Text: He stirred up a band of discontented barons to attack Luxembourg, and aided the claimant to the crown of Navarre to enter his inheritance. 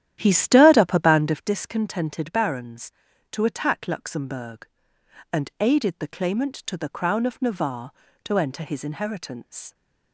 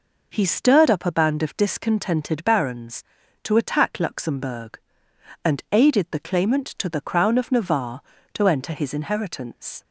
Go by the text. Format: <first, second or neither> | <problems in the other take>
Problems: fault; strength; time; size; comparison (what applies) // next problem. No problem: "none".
second | starts louder than the rest; strong; until 1.5 s; 11 dB